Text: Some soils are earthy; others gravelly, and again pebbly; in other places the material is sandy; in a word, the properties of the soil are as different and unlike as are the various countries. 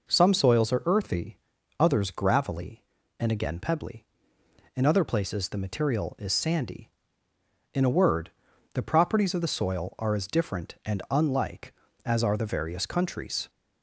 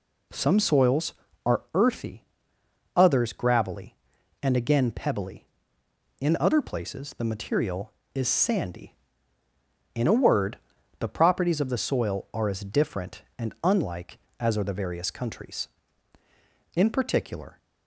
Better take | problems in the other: first | goes on to say "In particular"; noticeable; from 16.7 s on; 0.82 s long

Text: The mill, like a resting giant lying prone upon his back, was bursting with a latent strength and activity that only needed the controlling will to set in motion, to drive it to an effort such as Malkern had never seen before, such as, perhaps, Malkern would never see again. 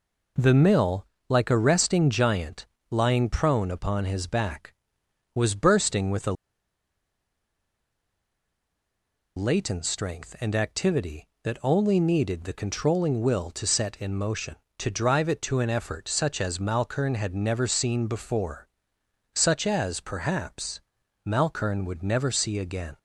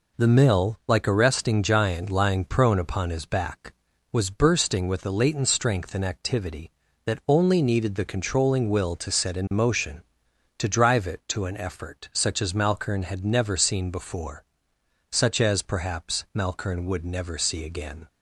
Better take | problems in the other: second | pauses between "giant" and "lying"; slight; at 2.6 s; 0.24 s long // pauses between "a" and "latent"; strong; at 6.3 s; 3.0 s long

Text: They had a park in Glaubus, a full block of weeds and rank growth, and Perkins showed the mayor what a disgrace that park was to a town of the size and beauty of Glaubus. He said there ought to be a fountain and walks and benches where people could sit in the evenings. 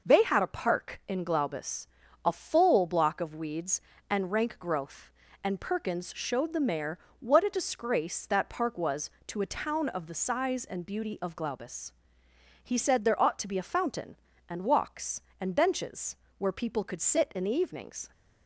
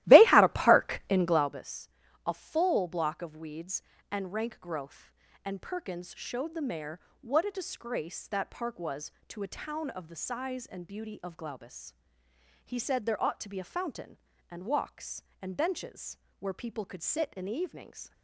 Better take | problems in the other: first | starts louder than the rest; strong; until 1.6 s; 16 dB // pauses between "mayor" and "what"; slight; at 6.9 s; 0.22 s long; slight in the first // pauses between "benches" and "where"; slight; at 16.1 s; 0.24 s long; slight in the first

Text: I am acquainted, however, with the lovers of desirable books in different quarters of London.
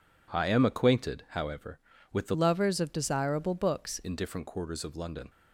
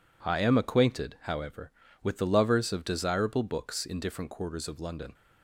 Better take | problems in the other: second | changes voice from "lovers" to "books"; from 2.3 to 3.9 s; 1.6 s long

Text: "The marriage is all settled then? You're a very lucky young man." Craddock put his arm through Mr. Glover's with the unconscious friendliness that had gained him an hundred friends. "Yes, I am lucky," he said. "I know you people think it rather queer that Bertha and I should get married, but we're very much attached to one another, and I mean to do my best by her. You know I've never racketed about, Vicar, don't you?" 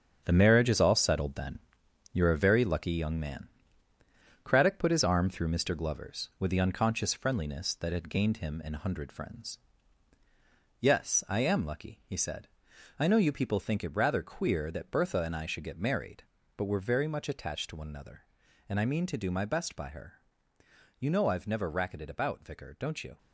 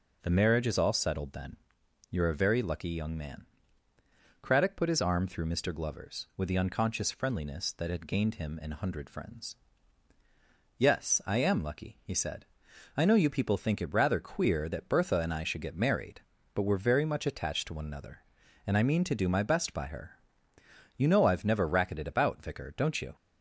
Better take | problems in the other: second | gets quieter; strong; throughout; 9 dB

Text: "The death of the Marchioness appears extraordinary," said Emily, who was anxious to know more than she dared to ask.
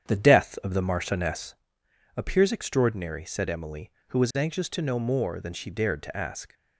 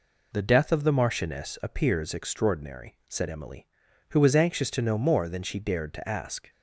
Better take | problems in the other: second | starts louder than the rest; strong; until 1.7 s; 8.5 dB // pauses between "Marchioness" and "appears"; noticeable; at 1.5 s; 0.64 s long

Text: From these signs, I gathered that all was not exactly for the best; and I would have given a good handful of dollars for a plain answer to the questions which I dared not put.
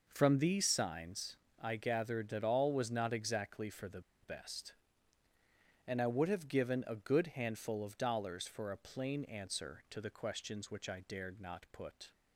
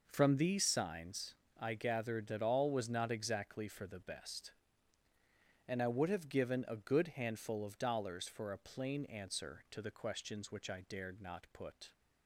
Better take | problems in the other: second | pauses between "the" and "best"; slight; at 3.9 s; 0.22 s long

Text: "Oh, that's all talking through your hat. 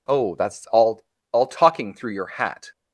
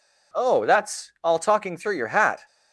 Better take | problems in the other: second | says "all" twice; at 1.3 s

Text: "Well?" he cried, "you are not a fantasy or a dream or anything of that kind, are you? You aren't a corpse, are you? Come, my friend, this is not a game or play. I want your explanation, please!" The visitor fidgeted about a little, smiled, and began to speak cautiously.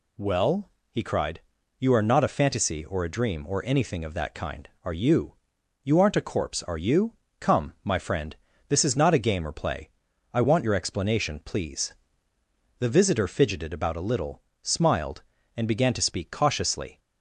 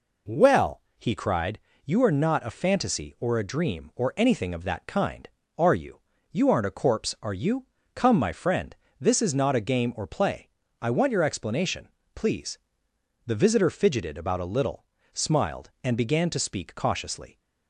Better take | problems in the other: neither | none

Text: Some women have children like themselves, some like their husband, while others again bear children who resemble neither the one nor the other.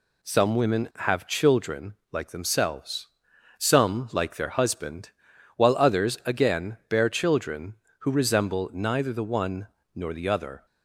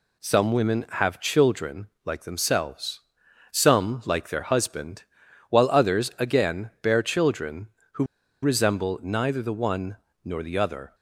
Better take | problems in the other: first | pauses between "children" and "like"; slight; at 1.8 s; 0.18 s long; slight in the first // pauses between "who" and "resemble"; at 8.0 s; 0.38 s long // pauses between "one" and "nor"; slight; at 9.9 s; 0.26 s long; slight in the first

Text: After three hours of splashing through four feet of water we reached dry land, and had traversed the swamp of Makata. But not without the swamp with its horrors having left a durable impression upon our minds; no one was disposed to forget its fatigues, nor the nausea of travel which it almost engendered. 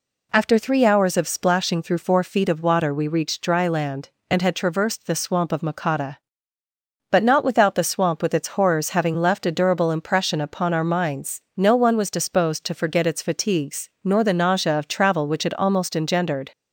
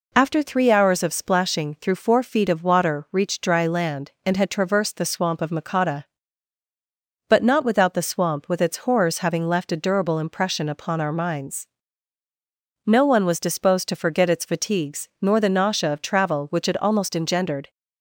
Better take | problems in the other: first | skips "we"; at 3.0 s

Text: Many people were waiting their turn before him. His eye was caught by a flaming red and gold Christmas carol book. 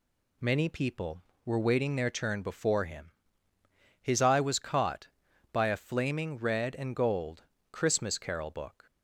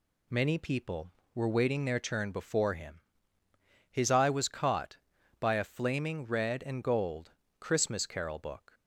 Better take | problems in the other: neither | pauses between "gold" and "Christmas"; slight; the same in both

